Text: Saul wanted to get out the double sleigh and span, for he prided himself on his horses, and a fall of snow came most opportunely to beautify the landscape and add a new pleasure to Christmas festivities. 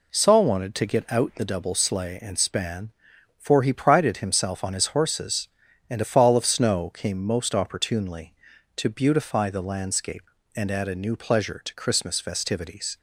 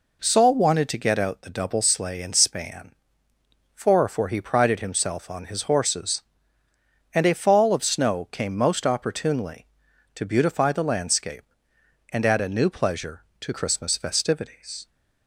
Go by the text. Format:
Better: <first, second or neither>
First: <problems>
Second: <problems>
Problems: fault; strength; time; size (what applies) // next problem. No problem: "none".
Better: first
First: none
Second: says "for" twice; at 4.0 s